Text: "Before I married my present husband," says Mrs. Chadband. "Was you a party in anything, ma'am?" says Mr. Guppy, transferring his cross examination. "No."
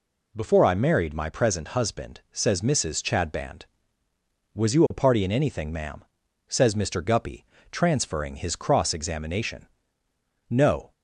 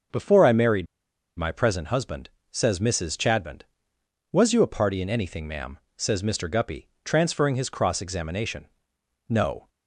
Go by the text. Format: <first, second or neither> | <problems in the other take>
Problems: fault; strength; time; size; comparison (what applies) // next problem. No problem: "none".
first | starts louder than the rest; until 1.6 s; 6 dB // pauses between "married" and "my"; noticeable; at 0.8 s; 0.52 s long